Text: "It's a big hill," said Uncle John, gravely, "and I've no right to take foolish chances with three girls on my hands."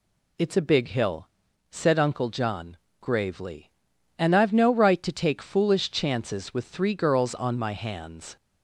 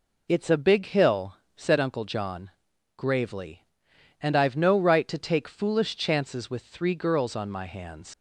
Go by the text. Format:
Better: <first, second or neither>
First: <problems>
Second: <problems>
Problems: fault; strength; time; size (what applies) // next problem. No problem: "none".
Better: first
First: none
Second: leaves "hands" unfinished; at 8.1 s; 75 ms